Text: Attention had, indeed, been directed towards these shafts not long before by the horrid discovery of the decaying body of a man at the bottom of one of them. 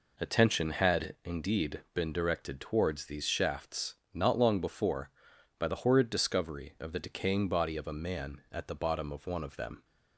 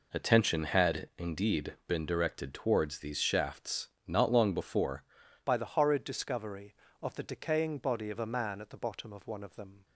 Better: first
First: pauses between "shafts" and "not"; slight; at 3.9 s; 0.20 s long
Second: pauses between "shafts" and "not"; slight; at 3.8 s; 0.20 s long // changes voice at "by"; from 5.4 s on; 4.4 s long

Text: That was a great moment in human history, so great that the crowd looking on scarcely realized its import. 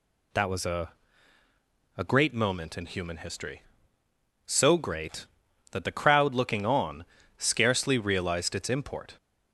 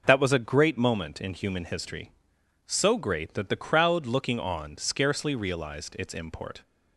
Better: second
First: says "a" twice; at 1.9 s // pauses between "on" and "scarcely"; slight; at 7.0 s; 0.32 s long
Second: none

